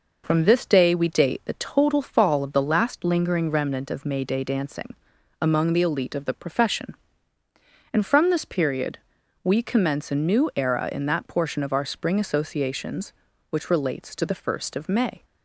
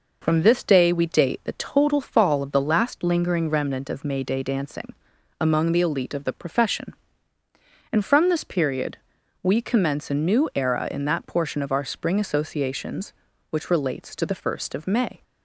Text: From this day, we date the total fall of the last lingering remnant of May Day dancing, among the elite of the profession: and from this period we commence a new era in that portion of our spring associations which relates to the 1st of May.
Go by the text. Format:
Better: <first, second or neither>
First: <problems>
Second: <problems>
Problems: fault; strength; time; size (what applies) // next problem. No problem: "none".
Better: neither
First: pauses between "period" and "we"; at 8.9 s; 0.44 s long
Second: pauses between "period" and "we"; at 8.9 s; 0.44 s long